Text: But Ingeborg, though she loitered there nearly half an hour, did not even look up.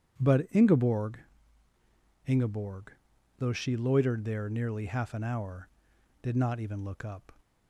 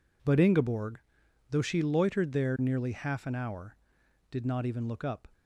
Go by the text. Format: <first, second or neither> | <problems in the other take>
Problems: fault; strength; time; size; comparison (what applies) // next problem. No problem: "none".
second | starts louder than the rest; strong; until 2.2 s; 9 dB // says "Ingeborg" twice; at 2.2 s